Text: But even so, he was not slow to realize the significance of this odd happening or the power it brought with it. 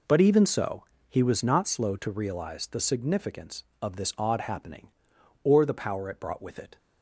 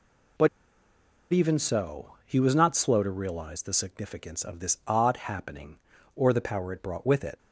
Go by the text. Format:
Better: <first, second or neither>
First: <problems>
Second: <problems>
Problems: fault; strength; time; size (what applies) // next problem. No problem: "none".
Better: first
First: none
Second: pauses between "But" and "even"; noticeable; at 0.4 s; 0.85 s long